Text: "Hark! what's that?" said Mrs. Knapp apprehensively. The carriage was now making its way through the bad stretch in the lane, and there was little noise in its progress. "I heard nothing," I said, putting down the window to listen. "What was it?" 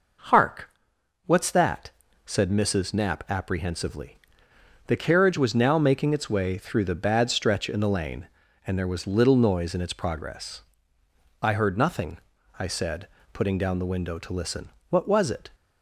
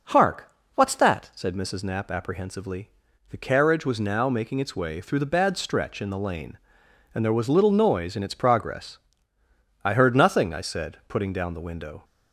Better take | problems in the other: first | stops before "to listen What was it"; at 12.0 s

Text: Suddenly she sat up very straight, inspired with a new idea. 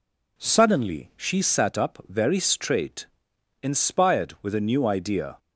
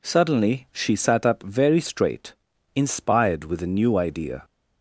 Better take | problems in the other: neither | none

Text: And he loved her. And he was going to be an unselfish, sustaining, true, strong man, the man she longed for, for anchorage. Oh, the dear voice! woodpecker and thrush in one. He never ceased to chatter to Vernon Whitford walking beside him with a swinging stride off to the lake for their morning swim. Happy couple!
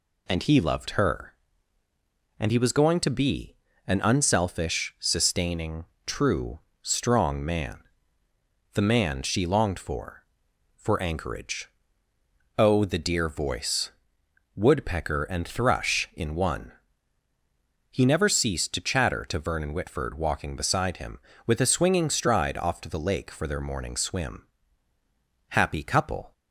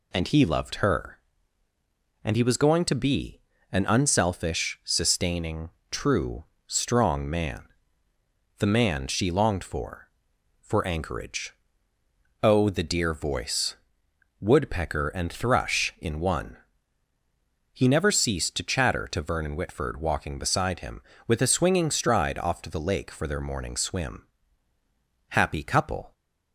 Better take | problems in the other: neither | pauses between "be" and "an"; slight; the same in both

